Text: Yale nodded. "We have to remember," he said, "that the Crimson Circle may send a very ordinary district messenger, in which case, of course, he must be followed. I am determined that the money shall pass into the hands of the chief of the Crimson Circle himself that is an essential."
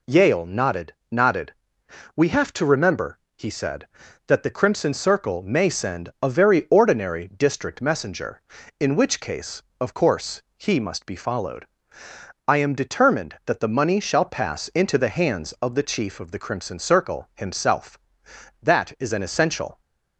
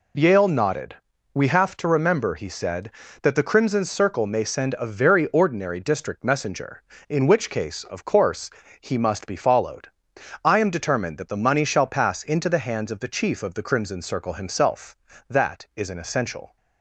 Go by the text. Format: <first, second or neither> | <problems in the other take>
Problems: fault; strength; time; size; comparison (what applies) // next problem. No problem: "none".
second | says "nodded" twice; at 1.0 s